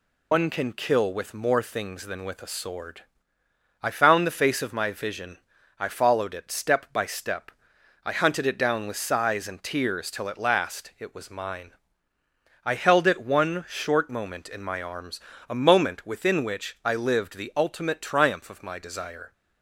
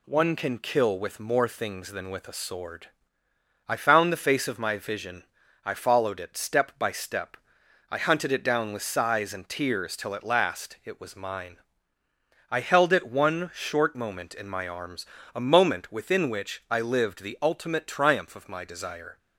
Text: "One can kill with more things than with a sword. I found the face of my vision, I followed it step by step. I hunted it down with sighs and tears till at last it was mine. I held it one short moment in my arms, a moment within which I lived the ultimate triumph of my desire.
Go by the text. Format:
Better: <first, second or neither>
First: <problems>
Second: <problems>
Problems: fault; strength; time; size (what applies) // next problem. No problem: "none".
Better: second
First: loses the start of "One"; at 0.3 s; 110 ms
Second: none